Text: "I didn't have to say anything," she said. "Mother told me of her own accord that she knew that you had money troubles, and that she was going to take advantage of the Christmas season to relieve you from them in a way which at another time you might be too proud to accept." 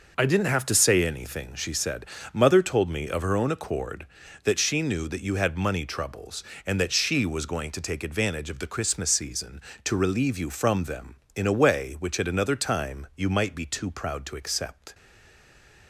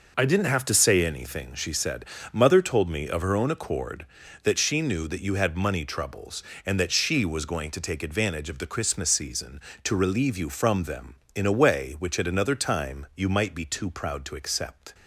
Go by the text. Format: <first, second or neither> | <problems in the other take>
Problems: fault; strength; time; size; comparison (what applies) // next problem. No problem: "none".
second | stays silent after the last word; slight; from 14.9 s on; 0.9 s long